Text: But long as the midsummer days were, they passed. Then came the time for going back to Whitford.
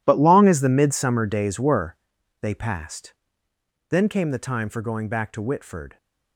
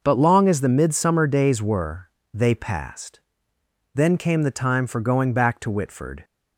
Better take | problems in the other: second | gets quieter; strong; throughout; 16 dB

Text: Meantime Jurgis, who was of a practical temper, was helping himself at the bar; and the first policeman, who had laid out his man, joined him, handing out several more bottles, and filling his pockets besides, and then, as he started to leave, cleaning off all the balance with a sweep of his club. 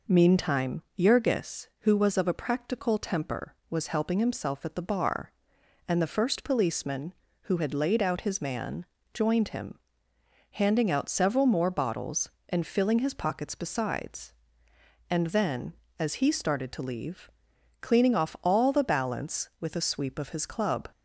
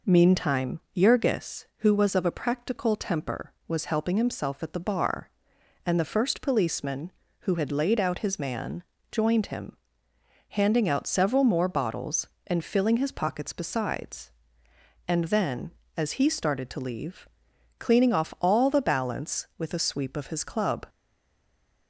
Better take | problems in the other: first | stays silent after the last word; from 20.8 s on; 1.0 s long

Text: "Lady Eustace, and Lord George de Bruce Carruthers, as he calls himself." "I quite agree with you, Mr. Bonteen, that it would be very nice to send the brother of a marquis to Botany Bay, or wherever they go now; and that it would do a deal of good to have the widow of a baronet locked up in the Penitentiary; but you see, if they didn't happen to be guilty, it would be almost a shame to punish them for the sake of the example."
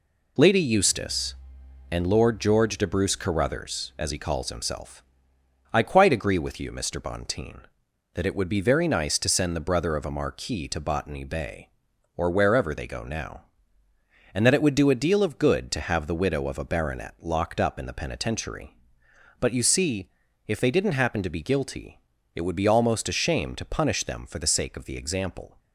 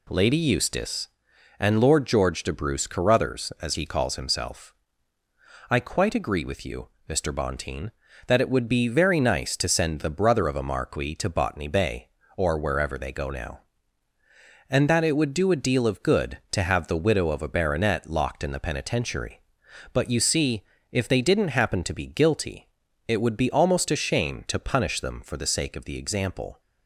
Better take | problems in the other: first | skips "up"; at 18.4 s

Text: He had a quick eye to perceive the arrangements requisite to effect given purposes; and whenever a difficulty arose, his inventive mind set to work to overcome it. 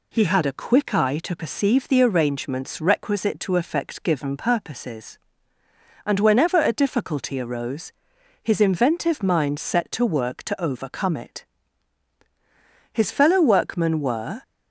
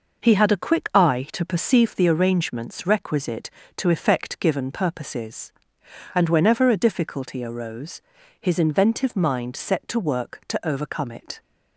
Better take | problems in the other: second | goes on to say "His fellow workmen were"; from 12.9 s on; 1.5 s long

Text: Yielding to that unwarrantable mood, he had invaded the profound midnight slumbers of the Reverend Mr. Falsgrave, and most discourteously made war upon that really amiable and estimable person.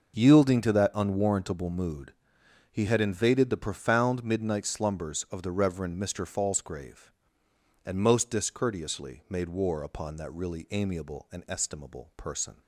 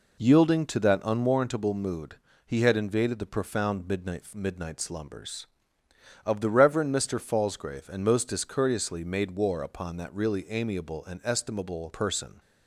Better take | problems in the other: first | says "midnight" twice; at 4.3 s

